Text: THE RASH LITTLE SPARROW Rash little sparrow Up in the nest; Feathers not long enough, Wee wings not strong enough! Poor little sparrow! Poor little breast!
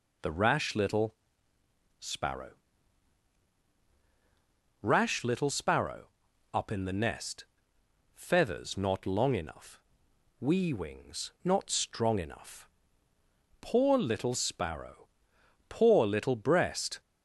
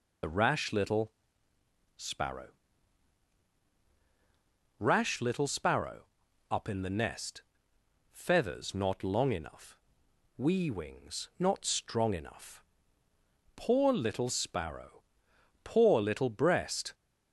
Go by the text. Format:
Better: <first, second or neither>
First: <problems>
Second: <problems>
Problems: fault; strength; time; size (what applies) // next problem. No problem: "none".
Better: first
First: pauses between "LITTLE" and "SPARROW"; noticeable; at 1.1 s; 0.86 s long // pauses between "SPARROW" and "Rash"; strong; at 2.4 s; 2.3 s long // pauses between "sparrow" and "Up"; at 6.0 s; 0.44 s long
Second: loses the start of "THE"; at 0.2 s; 40 ms // pauses between "LITTLE" and "SPARROW"; noticeable; at 1.1 s; 0.86 s long // pauses between "SPARROW" and "Rash"; strong; at 2.4 s; 2.3 s long // pauses between "sparrow" and "Up"; at 6.0 s; 0.44 s long